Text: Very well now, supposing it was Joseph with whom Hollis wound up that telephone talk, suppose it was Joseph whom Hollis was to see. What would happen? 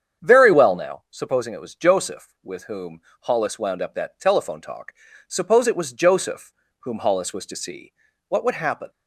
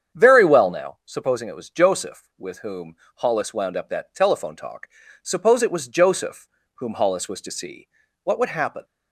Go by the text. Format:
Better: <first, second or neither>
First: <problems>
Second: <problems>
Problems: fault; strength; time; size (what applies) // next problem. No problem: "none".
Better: neither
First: starts louder than the rest; strong; until 1.3 s; 8 dB // pauses between "whom" and "Hollis"; slight; at 2.9 s; 0.22 s long // pauses between "Joseph" and "whom"; slight; at 6.5 s; 0.26 s long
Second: starts louder than the rest; strong; until 1.2 s; 8 dB // pauses between "whom" and "Hollis"; slight; at 2.9 s; 0.22 s long // pauses between "Joseph" and "whom"; slight; at 6.4 s; 0.26 s long